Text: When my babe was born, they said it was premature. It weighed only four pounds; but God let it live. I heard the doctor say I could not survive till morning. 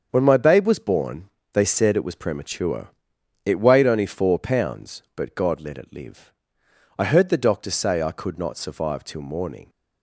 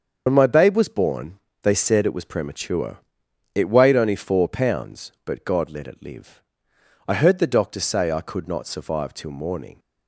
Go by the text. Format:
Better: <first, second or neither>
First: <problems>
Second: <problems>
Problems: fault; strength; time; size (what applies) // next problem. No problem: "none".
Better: first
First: starts louder than the rest; until 1.1 s; 7 dB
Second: loses the start of "When"; at 0.2 s; 55 ms // starts louder than the rest; until 1.2 s; 7 dB